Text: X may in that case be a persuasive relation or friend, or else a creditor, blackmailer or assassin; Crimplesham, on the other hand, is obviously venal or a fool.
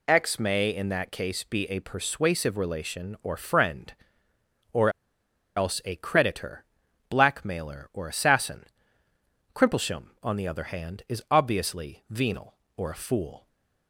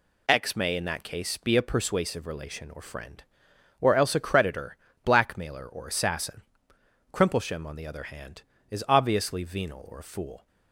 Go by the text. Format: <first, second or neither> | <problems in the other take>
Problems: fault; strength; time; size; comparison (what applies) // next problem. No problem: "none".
second | pauses between "or" and "else"; noticeable; at 4.8 s; 0.67 s long // stays silent after the last word; slight; from 13.3 s on; 0.5 s long